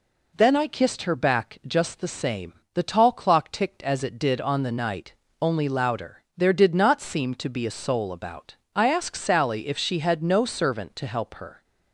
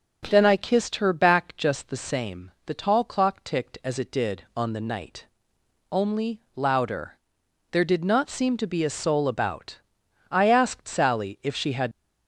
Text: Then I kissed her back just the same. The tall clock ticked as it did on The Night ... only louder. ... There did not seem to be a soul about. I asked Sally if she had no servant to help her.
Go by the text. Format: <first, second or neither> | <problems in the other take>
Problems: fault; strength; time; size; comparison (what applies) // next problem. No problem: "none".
first | starts louder than the rest; until 1.3 s; 6.5 dB // stops before "no servant to help her"; at 11.9 s